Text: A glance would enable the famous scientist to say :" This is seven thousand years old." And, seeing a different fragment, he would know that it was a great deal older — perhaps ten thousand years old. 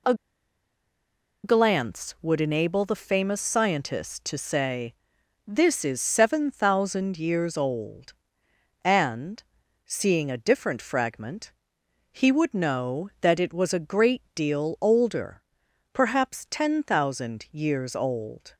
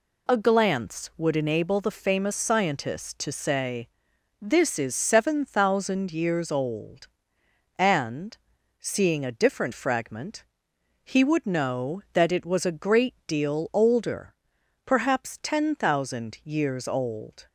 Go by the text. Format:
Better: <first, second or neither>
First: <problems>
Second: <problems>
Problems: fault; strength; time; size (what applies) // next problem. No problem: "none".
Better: second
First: pauses between "A" and "glance"; strong; at 0.1 s; 1.3 s long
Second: none